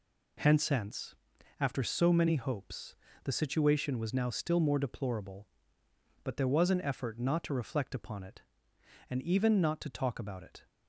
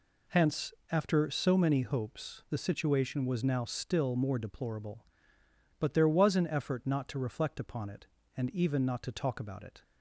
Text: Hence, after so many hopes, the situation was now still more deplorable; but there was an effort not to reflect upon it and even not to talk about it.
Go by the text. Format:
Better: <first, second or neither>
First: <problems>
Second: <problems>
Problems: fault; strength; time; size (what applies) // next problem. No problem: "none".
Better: second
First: says "Hence" twice; at 0.6 s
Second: none